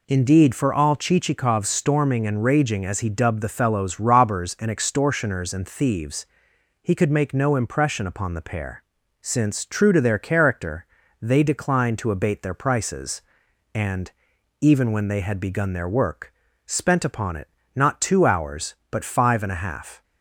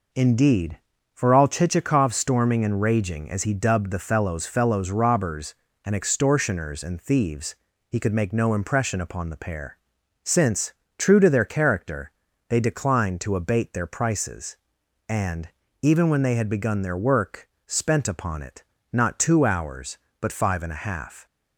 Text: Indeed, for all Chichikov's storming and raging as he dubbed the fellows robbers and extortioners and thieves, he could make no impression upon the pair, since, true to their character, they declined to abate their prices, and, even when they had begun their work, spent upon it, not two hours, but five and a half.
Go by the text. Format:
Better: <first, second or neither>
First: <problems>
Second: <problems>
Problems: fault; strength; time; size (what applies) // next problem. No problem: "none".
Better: first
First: none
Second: says "fellows" twice; at 4.4 s